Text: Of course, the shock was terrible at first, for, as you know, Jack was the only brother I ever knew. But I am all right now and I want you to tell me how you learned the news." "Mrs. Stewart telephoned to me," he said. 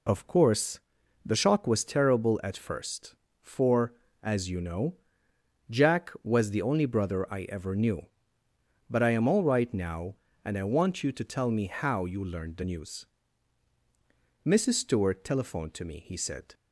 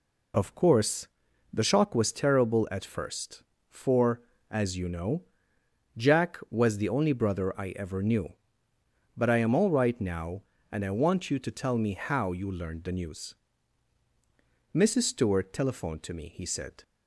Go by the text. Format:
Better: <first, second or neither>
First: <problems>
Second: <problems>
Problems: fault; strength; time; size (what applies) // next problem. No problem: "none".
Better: neither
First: none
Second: none